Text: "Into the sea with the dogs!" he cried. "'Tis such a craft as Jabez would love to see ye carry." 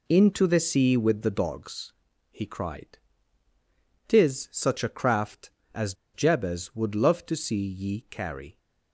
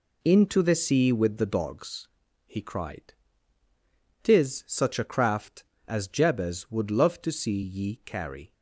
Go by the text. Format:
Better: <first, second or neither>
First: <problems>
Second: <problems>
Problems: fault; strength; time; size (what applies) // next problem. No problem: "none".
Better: second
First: pauses between "as" and "Jabez"; slight; at 5.9 s; 0.18 s long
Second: none